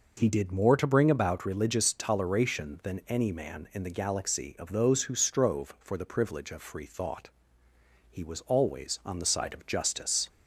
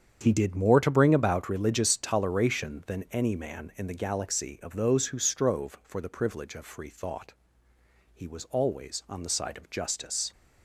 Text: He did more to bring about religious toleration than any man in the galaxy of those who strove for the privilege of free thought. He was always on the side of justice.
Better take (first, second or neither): first